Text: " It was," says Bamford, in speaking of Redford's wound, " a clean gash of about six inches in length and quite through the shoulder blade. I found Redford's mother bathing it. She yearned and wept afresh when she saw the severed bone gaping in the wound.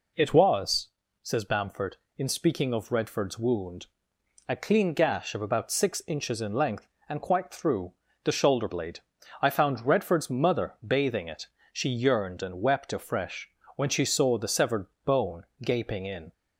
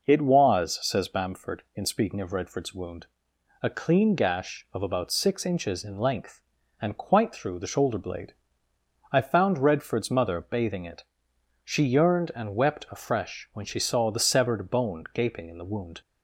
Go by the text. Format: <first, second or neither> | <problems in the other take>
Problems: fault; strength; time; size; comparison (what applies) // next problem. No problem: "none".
second | pauses between "through" and "the"; slight; at 7.9 s; 0.30 s long // pauses between "afresh" and "when"; slight; at 13.4 s; 0.28 s long // pauses between "severed" and "bone"; slight; at 14.8 s; 0.22 s long // pauses between "bone" and "gaping"; slight; at 15.4 s; 0.16 s long // stops before "the wound"; at 16.3 s